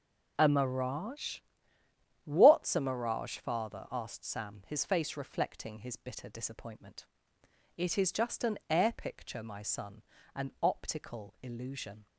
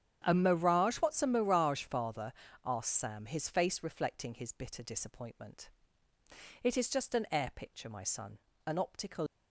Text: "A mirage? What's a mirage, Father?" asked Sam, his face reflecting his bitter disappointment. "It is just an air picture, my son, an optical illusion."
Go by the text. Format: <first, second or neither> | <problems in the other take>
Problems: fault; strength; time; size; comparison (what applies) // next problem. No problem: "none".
first | starts louder than the rest; strong; until 1.2 s; 9 dB // stops before "illusion"; at 9.2 s